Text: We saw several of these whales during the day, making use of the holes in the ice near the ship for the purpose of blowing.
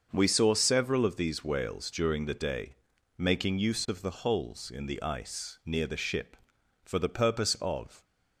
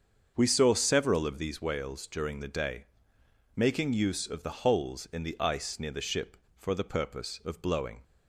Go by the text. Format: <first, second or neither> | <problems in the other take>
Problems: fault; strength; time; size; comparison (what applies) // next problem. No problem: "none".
second | starts louder than the rest; until 1.1 s; 6.5 dB; also in the second // stops before "blowing"; at 8.0 s